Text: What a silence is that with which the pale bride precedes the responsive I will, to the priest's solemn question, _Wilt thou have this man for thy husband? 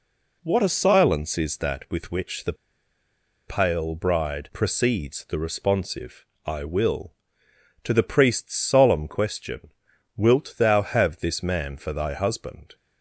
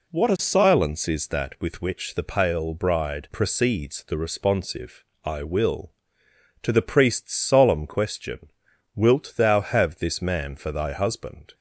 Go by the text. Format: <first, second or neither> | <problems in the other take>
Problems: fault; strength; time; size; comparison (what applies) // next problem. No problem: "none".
second | pauses between "the" and "pale"; noticeable; at 2.5 s; 0.94 s long // pauses between "responsive" and "I"; slight; at 6.2 s; 0.20 s long; slight in the second